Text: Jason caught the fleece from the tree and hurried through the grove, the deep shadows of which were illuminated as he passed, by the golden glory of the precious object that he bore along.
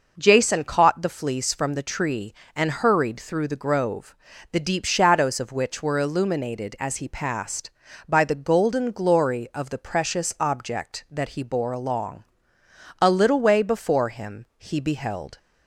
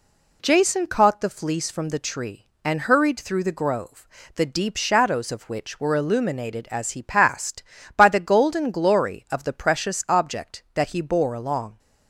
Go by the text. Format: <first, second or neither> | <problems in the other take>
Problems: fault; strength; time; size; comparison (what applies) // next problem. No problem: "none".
second | goes on to say "A little way before him he beheld"; strong; from 12.9 s on; 2.3 s long